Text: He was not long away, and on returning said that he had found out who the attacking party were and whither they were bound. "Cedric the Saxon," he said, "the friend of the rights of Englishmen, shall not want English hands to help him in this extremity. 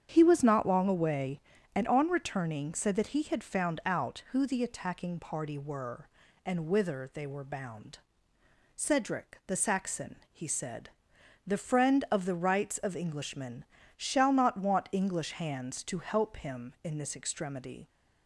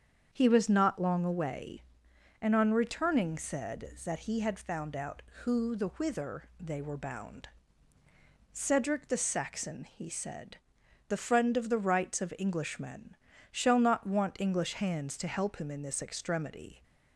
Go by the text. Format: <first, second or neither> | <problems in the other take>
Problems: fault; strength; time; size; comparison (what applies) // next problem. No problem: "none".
first | starts louder than the rest; strong; until 1.3 s; 7.5 dB; strong in the first // skips "attacking party were and"; at 5.8 s